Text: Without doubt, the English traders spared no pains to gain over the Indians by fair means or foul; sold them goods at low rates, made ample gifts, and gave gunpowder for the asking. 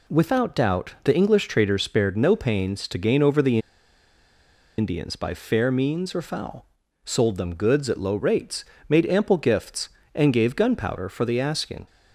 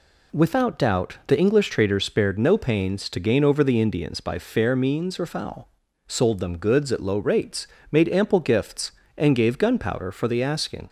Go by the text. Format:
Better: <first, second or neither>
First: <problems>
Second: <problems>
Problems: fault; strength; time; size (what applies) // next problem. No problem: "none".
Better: second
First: pauses between "the" and "Indians"; at 3.5 s; 1.1 s long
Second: none